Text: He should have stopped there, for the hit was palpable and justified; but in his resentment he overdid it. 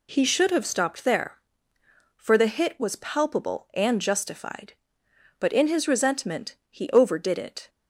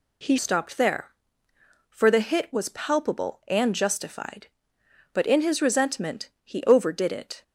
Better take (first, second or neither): first